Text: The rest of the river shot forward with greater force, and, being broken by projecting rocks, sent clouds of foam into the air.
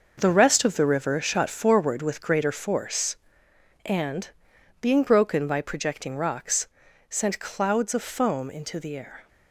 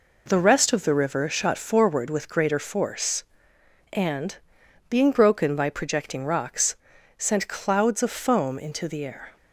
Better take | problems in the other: second | gets quieter; strong; throughout; 10 dB

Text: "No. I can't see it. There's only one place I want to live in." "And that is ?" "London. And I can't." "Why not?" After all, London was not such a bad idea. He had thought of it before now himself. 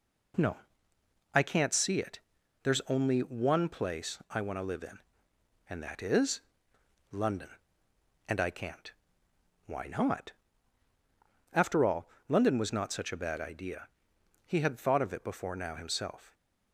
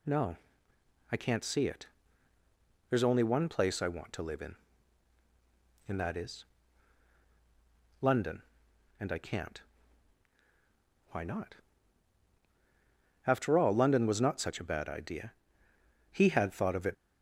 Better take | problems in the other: first | stops before "before now himself"; at 16.9 s

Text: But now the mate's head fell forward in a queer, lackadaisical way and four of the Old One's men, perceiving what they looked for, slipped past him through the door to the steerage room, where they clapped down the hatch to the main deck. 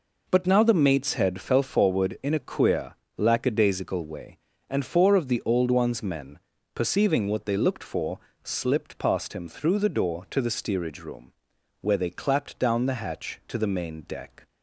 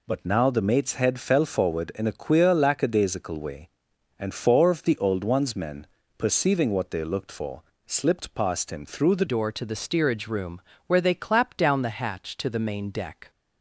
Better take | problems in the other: first | changes voice at "door"; from 9.2 s on; 4.0 s long

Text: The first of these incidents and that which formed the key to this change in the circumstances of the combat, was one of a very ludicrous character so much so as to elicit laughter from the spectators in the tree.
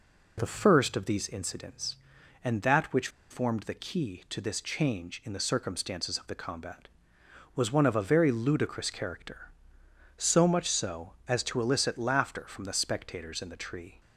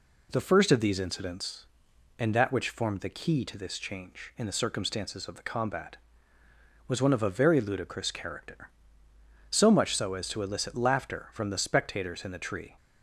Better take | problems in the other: second | pauses between "which" and "formed"; slight; at 3.0 s; 0.21 s long

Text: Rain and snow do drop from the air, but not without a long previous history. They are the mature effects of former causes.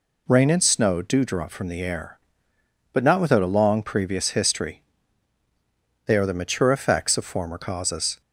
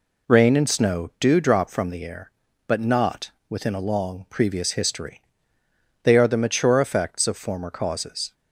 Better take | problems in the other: first | says "within" for "without"; at 3.4 s

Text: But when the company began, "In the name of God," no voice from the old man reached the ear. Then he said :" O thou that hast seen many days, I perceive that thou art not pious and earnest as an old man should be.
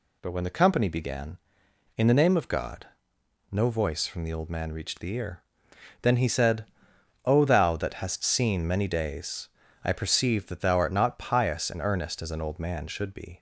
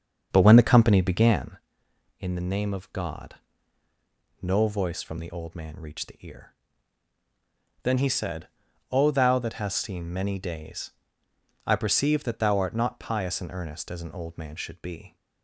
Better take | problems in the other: first | starts louder than the rest; strong; until 1.6 s; 7 dB

